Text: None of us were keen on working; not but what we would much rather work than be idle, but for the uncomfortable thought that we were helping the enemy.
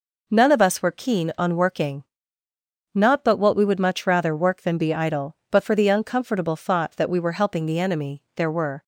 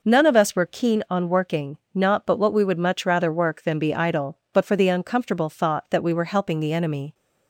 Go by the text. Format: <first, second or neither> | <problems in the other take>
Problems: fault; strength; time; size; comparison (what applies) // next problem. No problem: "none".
second | goes on to say "There were"; slight; from 8.3 s on; 0.48 s long